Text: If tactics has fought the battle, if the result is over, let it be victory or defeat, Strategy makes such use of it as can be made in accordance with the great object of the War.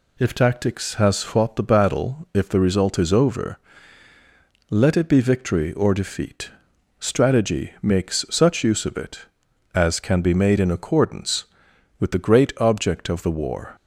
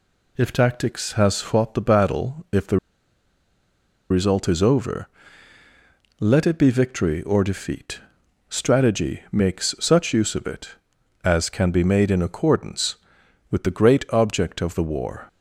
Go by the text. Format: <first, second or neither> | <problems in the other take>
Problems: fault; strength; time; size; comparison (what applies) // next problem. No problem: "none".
first | pauses between "the" and "result"; strong; at 2.7 s; 1.3 s long